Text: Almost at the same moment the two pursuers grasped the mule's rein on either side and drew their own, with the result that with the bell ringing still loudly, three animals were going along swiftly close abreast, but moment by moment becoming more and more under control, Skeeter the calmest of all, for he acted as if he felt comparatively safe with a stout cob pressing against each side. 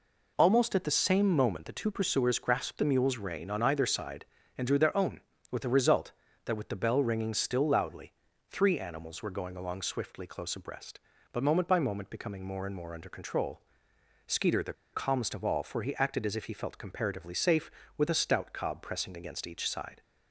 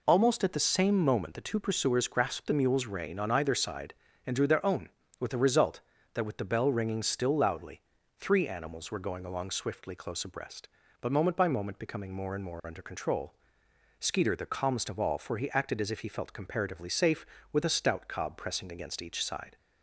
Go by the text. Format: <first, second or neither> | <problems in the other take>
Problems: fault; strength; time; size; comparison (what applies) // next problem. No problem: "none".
second | pauses between "the" and "calmest"; slight; at 14.7 s; 0.20 s long